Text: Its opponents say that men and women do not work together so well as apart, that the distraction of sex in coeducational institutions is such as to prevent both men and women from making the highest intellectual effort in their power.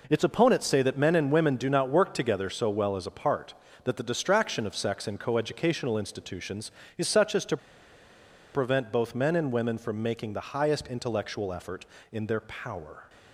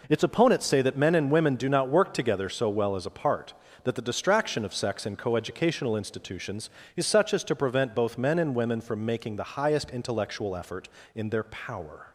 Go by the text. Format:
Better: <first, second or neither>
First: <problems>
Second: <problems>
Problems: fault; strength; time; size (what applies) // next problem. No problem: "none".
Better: second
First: pauses between "to" and "prevent"; noticeable; at 7.5 s; 0.96 s long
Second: none